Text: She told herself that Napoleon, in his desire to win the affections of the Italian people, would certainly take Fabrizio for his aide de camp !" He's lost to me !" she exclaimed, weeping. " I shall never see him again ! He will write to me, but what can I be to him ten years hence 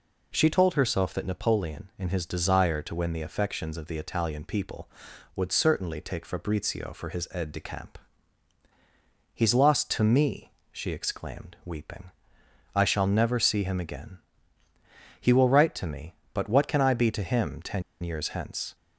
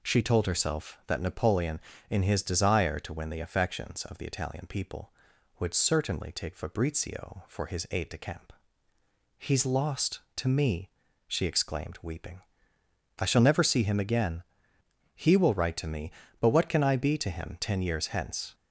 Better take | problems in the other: second | pauses between "ten" and "years"; slight; at 17.8 s; 0.20 s long

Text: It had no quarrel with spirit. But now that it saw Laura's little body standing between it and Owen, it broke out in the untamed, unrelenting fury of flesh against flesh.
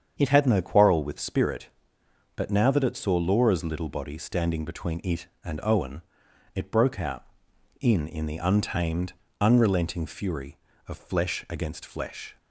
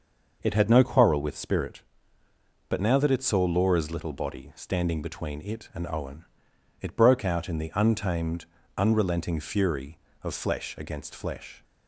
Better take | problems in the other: second | starts louder than the rest; strong; until 1.2 s; 7.5 dB // says "in" twice; at 8.0 s

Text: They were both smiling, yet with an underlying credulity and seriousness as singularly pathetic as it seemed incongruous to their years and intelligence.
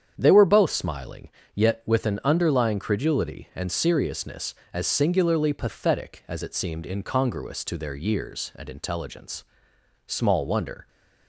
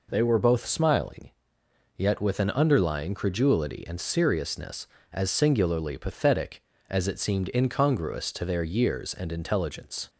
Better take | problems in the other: second | starts louder than the rest; strong; until 1.1 s; 8.5 dB // goes on to say "Small wonder"; noticeable; from 10.0 s on; 0.82 s long

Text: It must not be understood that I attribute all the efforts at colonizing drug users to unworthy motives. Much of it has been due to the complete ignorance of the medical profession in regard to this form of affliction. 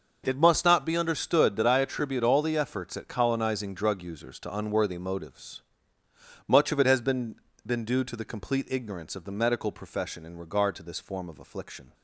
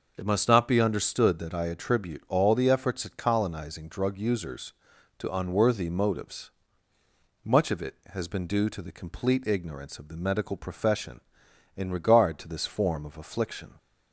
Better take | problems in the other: second | says "been" twice; at 7.6 s

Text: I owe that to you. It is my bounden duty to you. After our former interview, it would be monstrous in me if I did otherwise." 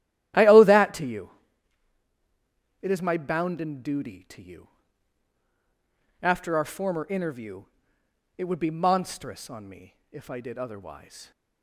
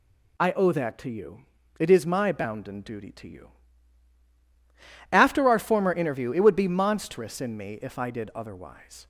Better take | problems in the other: second | starts louder than the rest; strong; until 2.8 s; 13 dB // says "on" for "in"; at 9.4 s // pauses between "me" and "if"; slight; at 9.9 s; 0.16 s long

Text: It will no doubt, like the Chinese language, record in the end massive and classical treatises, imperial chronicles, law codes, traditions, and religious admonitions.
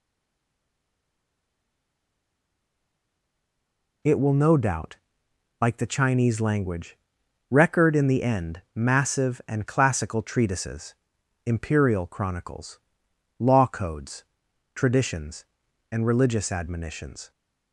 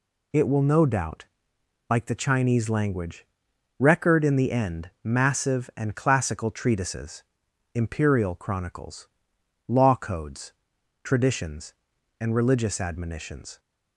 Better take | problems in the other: second | stays silent before the first word; strong; until 4.0 s; 4.0 s long

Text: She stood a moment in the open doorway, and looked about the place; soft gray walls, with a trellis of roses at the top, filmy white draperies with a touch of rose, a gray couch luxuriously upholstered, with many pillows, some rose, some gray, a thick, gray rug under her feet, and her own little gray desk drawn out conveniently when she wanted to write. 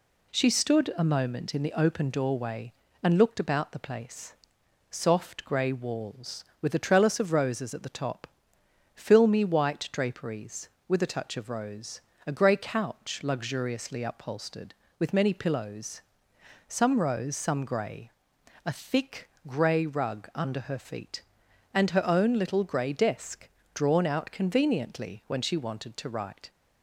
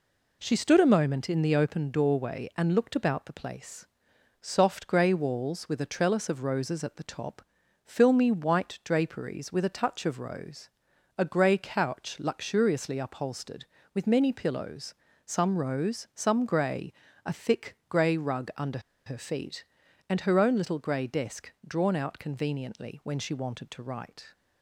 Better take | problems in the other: first | pauses between "under" and "her"; slight; at 18.7 s; 0.26 s long // pauses between "desk" and "drawn"; slight; at 21.5 s; 0.16 s long; slight in the first

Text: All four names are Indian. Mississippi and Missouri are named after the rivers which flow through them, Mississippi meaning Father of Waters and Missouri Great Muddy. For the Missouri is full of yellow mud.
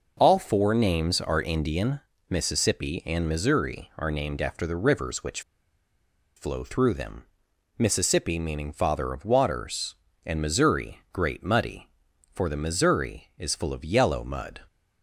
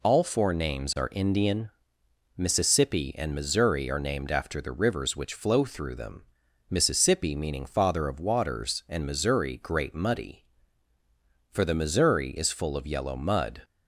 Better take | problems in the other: second | pauses between "which" and "flow"; noticeable; at 5.4 s; 0.96 s long

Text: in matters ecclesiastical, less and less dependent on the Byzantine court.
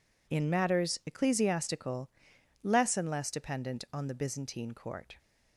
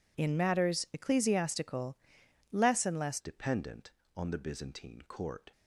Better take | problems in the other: first | changes voice at "dependent"; from 3.1 s on; 2.4 s long

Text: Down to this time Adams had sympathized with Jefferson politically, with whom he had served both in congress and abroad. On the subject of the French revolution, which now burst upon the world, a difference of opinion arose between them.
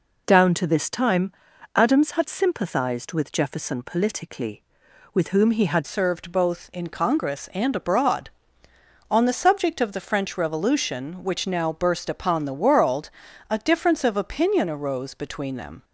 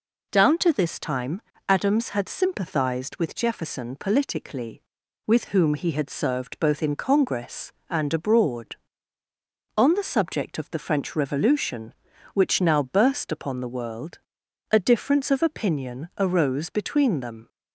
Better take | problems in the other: second | pauses between "time" and "Adams"; at 1.3 s; 0.44 s long; slight in the second // changes voice at "served"; from 5.8 s on; 10.0 s long

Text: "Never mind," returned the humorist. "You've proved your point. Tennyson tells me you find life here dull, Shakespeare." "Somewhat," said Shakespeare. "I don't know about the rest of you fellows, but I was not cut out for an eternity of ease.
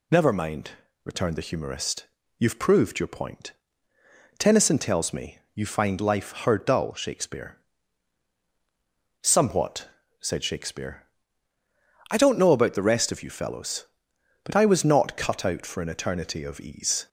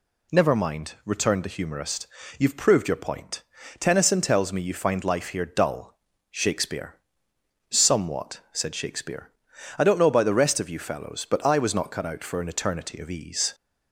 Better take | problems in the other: second | pauses between "me" and "you"; slight; at 5.3 s; 0.16 s long // says "her" for "here"; at 6.4 s

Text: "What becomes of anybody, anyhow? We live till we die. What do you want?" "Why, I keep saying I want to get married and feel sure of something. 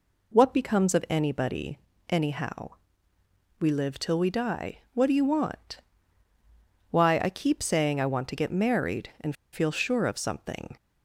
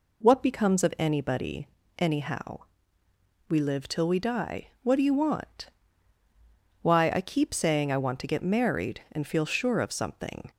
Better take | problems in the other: second | pauses between "and" and "feel"; slight; at 9.3 s; 0.18 s long

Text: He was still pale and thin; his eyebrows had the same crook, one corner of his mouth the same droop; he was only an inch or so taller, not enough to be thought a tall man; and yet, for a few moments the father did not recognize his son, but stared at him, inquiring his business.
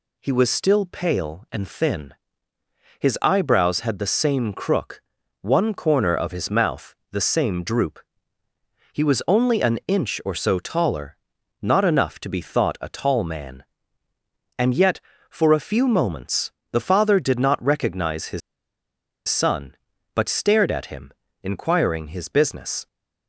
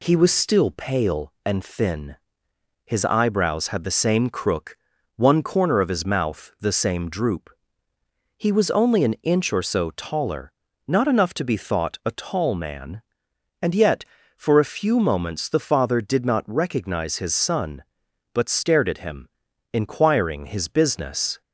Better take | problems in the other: second | pauses between "mouth" and "the"; slight; at 6.9 s; 0.20 s long // pauses between "moments" and "the"; slight; at 16.5 s; 0.22 s long // pauses between "his" and "son"; noticeable; at 18.4 s; 0.88 s long

